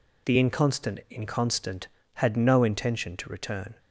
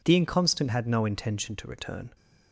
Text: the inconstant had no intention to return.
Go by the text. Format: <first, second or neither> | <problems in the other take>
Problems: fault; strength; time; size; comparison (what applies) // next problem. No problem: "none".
second | says "inconstant" twice; at 1.0 s